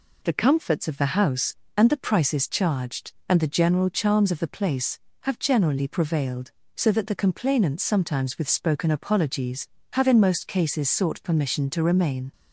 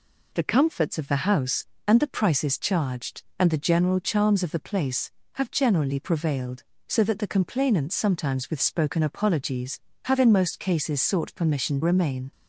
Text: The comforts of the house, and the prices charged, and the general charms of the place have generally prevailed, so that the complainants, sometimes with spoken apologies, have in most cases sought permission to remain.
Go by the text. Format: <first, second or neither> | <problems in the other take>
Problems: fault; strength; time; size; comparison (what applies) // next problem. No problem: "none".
first | skips "to"; at 11.8 s